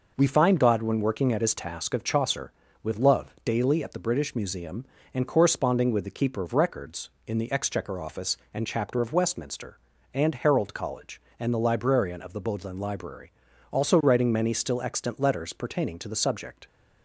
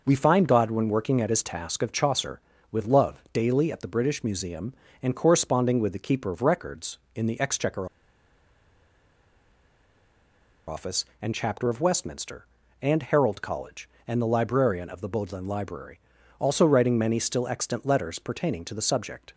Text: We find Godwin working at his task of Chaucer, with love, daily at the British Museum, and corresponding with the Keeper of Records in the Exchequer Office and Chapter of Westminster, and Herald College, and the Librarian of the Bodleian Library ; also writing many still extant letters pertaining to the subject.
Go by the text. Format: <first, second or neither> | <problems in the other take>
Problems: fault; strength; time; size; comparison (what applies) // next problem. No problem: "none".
first | pauses between "Exchequer" and "Office"; strong; at 7.8 s; 2.8 s long